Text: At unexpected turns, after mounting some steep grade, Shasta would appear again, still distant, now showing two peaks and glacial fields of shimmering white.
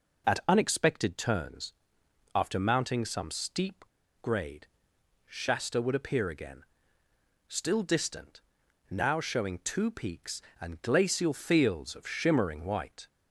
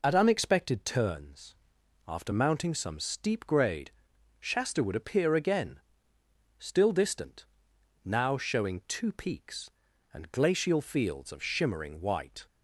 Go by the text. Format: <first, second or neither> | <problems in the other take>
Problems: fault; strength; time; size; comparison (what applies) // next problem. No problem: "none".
second | pauses between "steep" and "grade"; at 3.8 s; 0.36 s long